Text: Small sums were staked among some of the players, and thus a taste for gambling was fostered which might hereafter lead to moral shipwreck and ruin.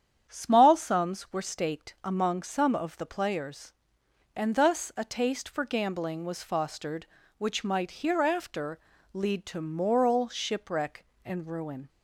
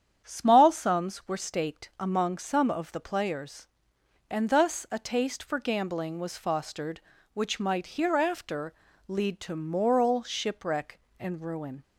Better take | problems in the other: neither | starts louder than the rest; strong; the same in both // pauses between "hereafter" and "lead"; slight; the same in both

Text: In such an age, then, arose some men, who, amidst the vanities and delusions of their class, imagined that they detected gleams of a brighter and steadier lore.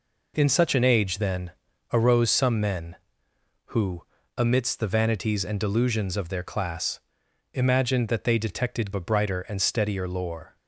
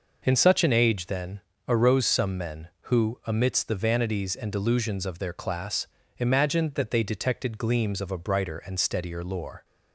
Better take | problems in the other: second | skips "gleams of"; at 8.9 s

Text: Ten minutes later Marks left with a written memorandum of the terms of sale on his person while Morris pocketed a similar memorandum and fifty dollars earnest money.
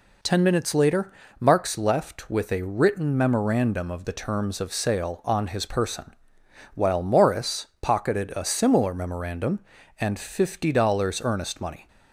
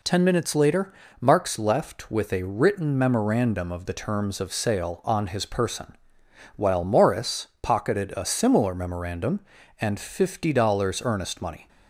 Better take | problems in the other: neither | pauses between "later" and "Marks"; slight; the same in both // pauses between "person" and "while"; noticeable; the same in both

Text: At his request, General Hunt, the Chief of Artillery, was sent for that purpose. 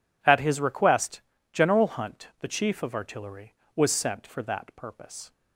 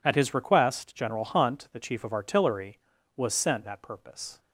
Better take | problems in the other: first | skips "for"; at 3.6 s

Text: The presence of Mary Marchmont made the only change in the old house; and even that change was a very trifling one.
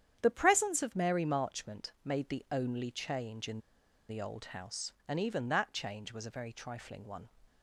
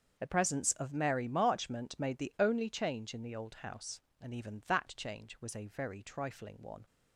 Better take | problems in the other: second | starts louder than the rest; strong; until 1.2 s; 9.5 dB; also in the second // pauses between "in" and "the"; noticeable; at 3.6 s; 0.48 s long

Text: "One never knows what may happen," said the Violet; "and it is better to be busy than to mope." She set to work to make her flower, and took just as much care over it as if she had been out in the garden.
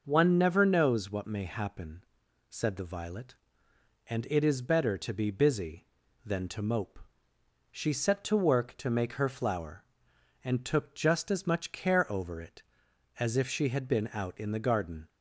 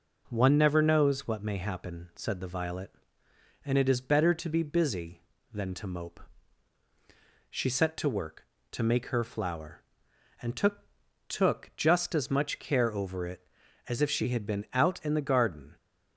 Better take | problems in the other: first | says "took" twice; at 11.2 s

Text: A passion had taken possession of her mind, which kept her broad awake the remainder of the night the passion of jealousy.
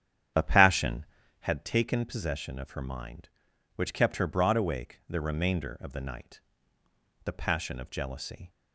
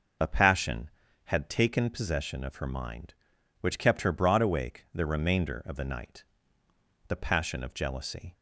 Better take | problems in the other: second | starts louder than the rest; strong; until 1.5 s; 9 dB // pauses between "night" and "the"; noticeable; at 6.3 s; 0.86 s long; noticeable in the second

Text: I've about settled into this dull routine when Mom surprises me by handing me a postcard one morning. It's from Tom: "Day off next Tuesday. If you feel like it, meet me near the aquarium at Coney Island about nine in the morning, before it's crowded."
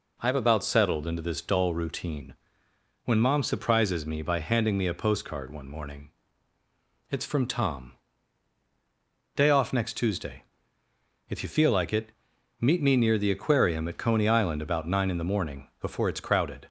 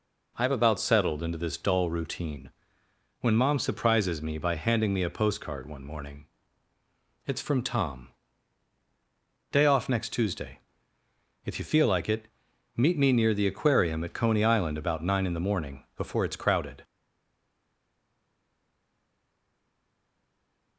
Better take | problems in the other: first | pauses between "routine" and "when"; noticeable; at 2.4 s; 0.70 s long; noticeable in the first // stays silent after the last word; strong; from 16.8 s on; 3.9 s long

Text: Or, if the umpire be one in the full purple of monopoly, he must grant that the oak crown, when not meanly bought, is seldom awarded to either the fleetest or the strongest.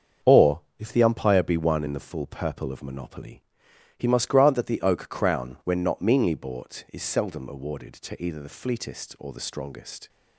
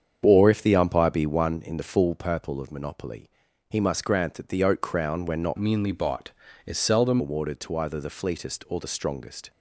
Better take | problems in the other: first | starts louder than the rest; strong; until 1.2 s; 7.5 dB; also in the first // changes voice from "meanly" to "seldom"; from 5.5 to 7.2 s; 1.7 s long

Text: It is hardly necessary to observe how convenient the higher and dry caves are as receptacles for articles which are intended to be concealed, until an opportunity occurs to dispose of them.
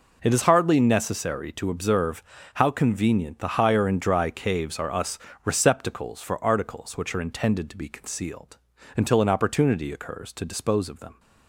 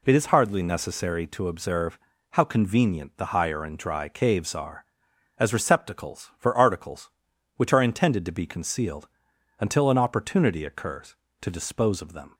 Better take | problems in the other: second | pauses between "observe" and "how"; slight; at 2.2 s; 0.34 s long; slight in the second // says "us" for "as"; at 4.9 s

